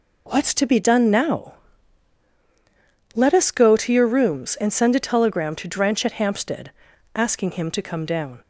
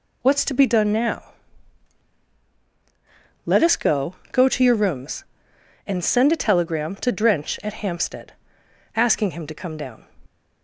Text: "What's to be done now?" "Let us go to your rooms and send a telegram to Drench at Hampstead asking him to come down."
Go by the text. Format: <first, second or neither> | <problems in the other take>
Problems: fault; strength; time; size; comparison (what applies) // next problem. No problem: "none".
first | says "go" twice; at 4.3 s // pauses between "Hampstead" and "asking"; noticeable; at 8.3 s; 0.62 s long; also in the first